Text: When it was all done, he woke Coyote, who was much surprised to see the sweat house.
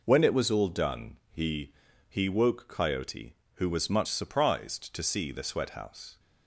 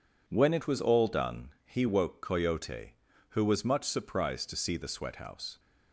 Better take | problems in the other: second | says "he" twice; at 2.0 s

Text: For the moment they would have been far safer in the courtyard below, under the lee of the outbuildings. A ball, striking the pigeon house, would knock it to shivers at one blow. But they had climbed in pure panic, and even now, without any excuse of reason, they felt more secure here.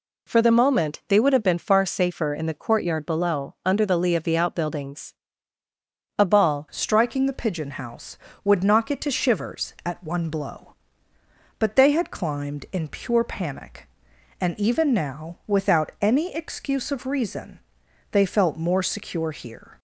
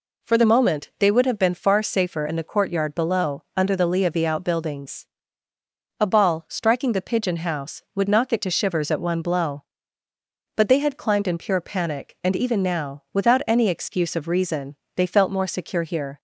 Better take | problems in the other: second | changes voice at "striking"; from 6.7 s on; 13.0 s long

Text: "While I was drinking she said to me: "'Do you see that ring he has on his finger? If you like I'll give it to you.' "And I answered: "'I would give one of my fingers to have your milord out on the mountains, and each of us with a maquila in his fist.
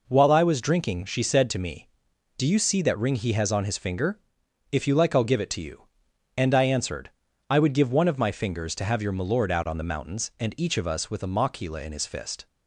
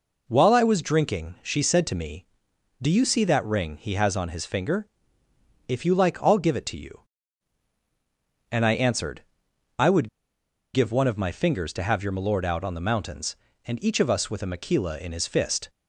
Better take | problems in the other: first | pauses between "would" and "give"; noticeable; at 10.0 s; 0.65 s long

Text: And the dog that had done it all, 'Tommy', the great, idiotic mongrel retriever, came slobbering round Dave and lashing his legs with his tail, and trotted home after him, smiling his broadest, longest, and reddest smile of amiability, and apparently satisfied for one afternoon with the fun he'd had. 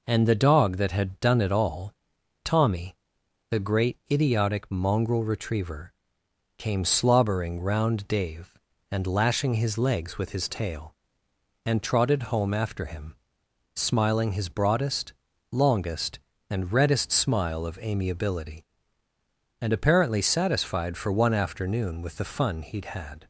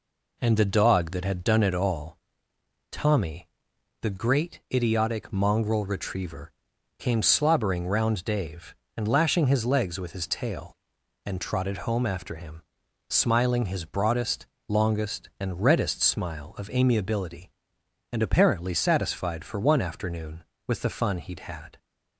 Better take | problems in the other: neither | none

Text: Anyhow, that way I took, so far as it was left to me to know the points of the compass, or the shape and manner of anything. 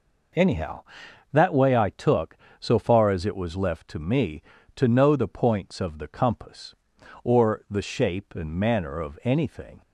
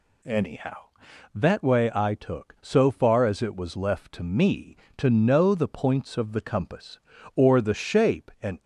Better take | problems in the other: first | stops before "manner of anything"; at 8.6 s

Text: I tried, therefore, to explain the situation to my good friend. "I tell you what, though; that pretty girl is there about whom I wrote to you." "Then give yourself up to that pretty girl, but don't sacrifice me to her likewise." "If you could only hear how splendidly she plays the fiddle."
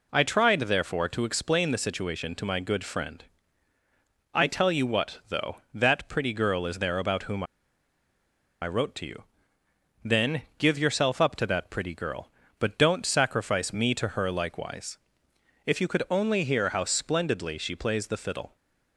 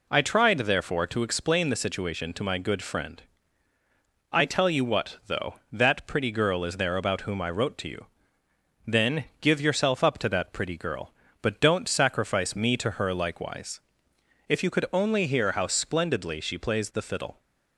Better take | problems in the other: second | pauses between "whom" and "I"; at 7.4 s; 1.1 s long // pauses between "Then" and "give"; slight; at 10.4 s; 0.16 s long; slight in the second

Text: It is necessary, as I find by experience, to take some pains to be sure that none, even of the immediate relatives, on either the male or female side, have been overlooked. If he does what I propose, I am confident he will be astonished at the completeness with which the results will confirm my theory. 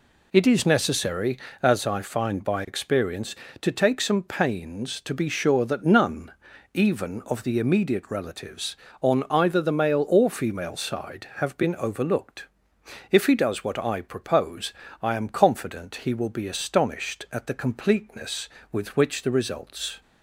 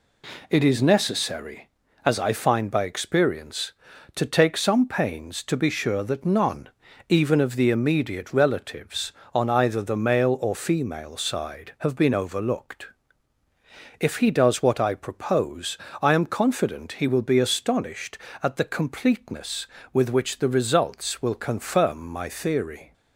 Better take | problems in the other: second | stops before "will confirm my theory"; at 20.0 s

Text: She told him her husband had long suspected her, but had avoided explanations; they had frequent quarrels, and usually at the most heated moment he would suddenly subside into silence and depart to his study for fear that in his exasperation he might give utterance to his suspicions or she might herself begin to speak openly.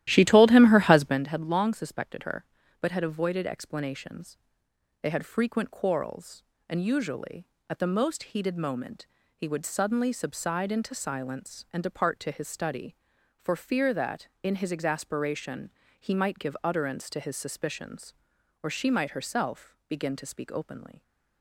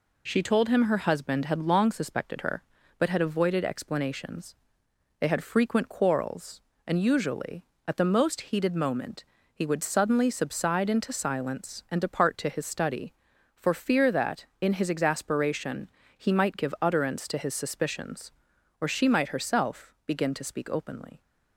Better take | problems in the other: second | starts louder than the rest; strong; until 1.2 s; 13.5 dB // pauses between "moment" and "he"; slight; at 9.0 s; 0.32 s long; slight in the second // pauses between "exasperation" and "he"; slight; at 15.7 s; 0.30 s long; slight in the second

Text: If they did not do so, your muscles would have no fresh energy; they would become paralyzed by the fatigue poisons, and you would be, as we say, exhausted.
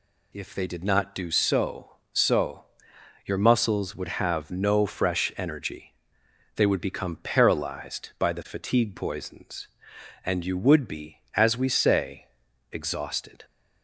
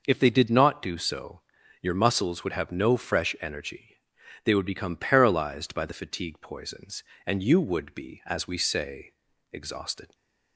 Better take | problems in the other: second | says "so" twice; at 2.1 s

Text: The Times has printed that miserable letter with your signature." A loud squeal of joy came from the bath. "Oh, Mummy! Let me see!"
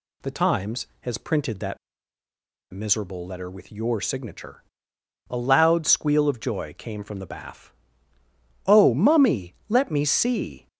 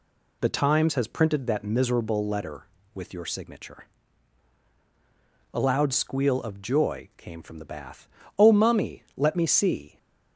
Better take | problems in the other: second | pauses between "that" and "miserable"; noticeable; at 1.7 s; 0.93 s long

